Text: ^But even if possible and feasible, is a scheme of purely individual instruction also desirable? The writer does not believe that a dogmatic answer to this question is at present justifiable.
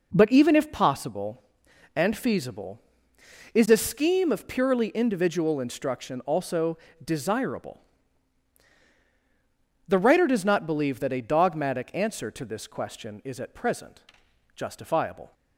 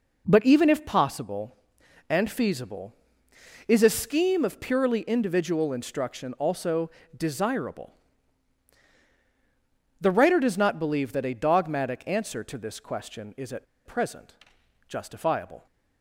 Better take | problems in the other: first | pauses between "also" and "desirable"; slight; at 6.8 s; 0.30 s long; slight in the first // pauses between "at" and "present"; slight; at 13.6 s; 0.20 s long // pauses between "present" and "justifiable"; noticeable; at 14.3 s; 0.54 s long; noticeable in the first

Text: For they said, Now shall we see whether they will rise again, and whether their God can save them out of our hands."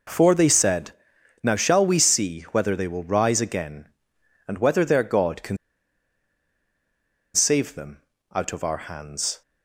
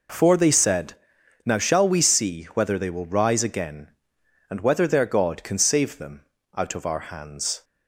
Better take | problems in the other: second | pauses between "can" and "save"; strong; at 5.5 s; 1.7 s long // pauses between "them" and "out"; slight; at 8.0 s; 0.32 s long; slight in the second

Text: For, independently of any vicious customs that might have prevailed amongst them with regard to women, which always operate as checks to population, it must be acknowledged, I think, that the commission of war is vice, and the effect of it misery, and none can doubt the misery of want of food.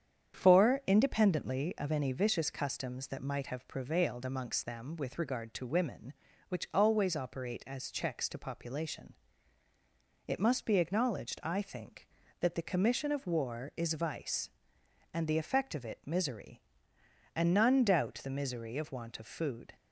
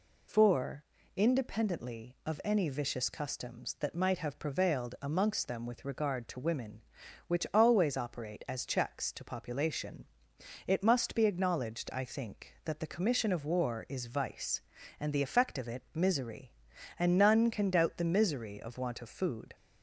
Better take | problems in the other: second | starts louder than the rest; strong; until 1.3 s; 8.5 dB // skips "can"; at 17.8 s

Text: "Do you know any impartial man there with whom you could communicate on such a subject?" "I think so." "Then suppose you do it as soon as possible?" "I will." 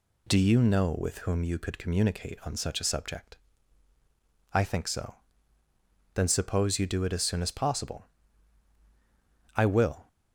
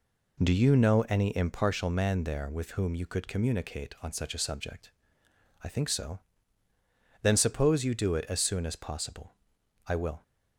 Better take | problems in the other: second | skips "any impartial man there"; at 0.9 s

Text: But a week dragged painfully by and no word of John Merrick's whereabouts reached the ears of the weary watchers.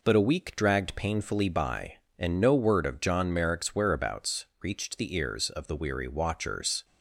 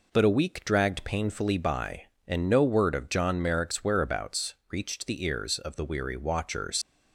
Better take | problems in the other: first | pauses between "whereabouts" and "reached"; slight; at 4.5 s; 0.18 s long; slight in the first // leaves "watchers" unfinished; at 6.8 s; 120 ms

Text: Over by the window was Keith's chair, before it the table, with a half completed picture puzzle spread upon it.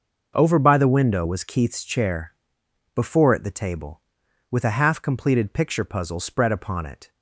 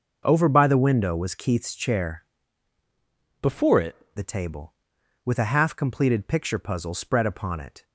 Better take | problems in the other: first | starts louder than the rest; noticeable; until 1.2 s; 6 dB // changes voice from "before" to "it"; from 3.4 to 3.9 s; 0.5 s long

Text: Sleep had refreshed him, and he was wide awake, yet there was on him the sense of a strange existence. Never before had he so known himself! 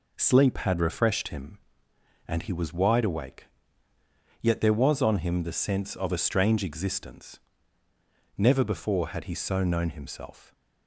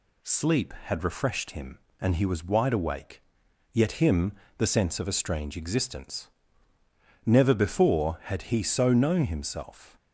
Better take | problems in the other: first | skips "there was on"; at 4.0 s // pauses between "him" and "the"; slight; at 4.3 s; 0.26 s long

